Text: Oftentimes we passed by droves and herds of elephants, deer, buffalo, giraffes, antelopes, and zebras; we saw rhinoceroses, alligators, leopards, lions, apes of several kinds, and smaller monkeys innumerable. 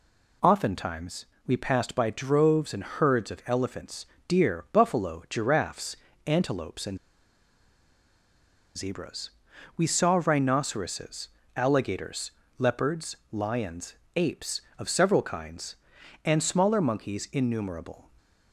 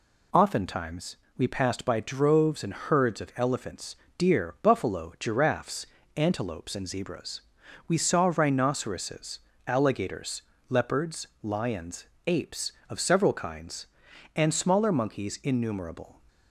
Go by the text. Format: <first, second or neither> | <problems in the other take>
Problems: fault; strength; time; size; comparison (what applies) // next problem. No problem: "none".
second | pauses between "Oftentimes" and "we"; slight; at 1.2 s; 0.22 s long; slight in the second // pauses between "and" and "zebras"; strong; at 6.9 s; 1.7 s long